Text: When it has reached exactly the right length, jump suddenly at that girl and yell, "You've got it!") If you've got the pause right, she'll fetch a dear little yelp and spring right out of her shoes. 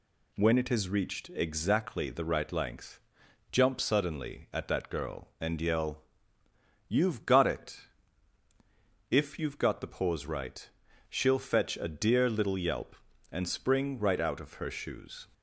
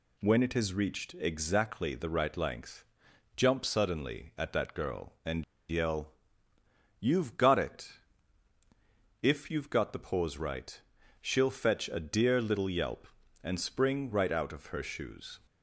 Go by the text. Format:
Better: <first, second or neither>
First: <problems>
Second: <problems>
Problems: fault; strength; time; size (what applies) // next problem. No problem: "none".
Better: first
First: none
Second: pauses between "and" and "yell"; slight; at 5.4 s; 0.26 s long